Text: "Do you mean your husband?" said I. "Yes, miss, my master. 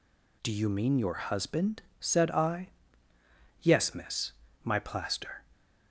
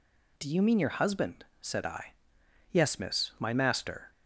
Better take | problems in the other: second | says "plaster" for "master"; at 4.7 s

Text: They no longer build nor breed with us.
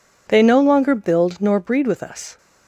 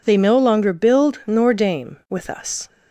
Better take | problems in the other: first | says "dame" for "breed"; at 1.5 s

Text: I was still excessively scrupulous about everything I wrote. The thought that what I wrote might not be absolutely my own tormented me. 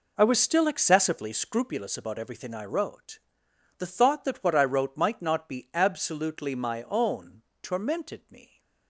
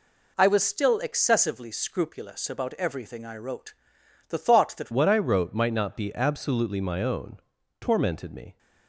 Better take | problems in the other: first | changes voice at "what"; from 4.9 s on; 3.6 s long // pauses between "own" and "tormented"; at 7.3 s; 0.42 s long; slight in the first

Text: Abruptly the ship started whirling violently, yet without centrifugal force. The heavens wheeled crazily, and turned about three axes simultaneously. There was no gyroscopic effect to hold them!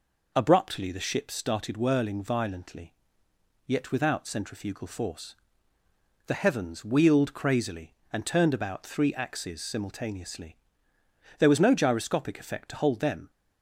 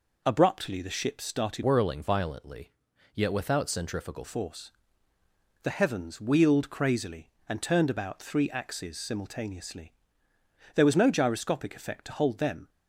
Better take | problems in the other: first | changes voice from "whirling" to "centrifugal"; from 1.6 to 4.2 s; 2.6 s long

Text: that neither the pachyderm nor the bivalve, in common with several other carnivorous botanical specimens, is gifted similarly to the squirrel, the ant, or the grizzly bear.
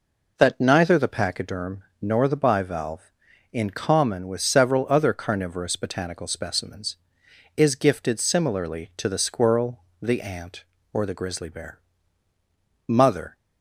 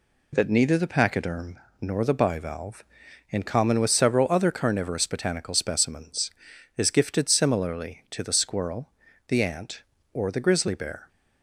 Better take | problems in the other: second | pauses between "pachyderm" and "nor"; slight; at 1.8 s; 0.18 s long; slight in the second // goes on to say "Mother"; slight; from 12.8 s on; 0.48 s long

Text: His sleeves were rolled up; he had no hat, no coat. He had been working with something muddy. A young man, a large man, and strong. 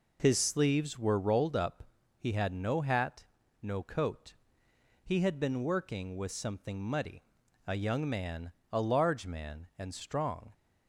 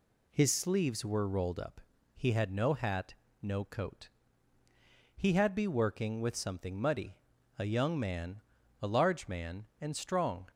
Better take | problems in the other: first | says "be" for "been"; at 5.5 s

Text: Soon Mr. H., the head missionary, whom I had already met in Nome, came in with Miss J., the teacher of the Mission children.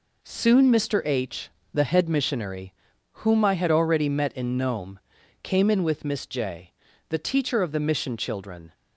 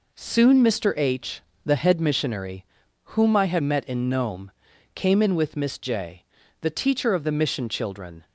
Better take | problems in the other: first | skips "already"; at 3.6 s

